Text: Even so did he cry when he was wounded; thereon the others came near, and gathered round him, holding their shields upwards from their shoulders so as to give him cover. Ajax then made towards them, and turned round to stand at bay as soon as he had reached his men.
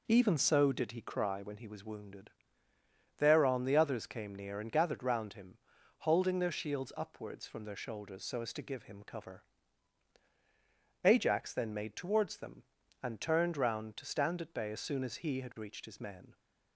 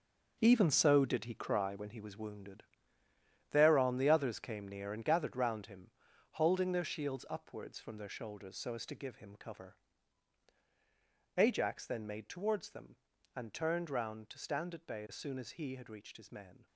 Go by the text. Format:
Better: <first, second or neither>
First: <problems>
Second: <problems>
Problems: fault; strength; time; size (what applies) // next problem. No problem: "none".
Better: first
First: none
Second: gets quieter; strong; throughout; 10.5 dB